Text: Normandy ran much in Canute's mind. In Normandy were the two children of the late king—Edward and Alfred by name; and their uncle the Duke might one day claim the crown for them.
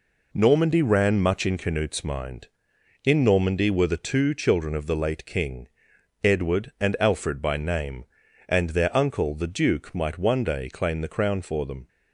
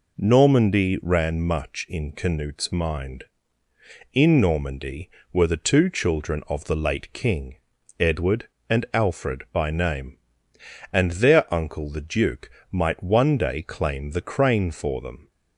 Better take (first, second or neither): first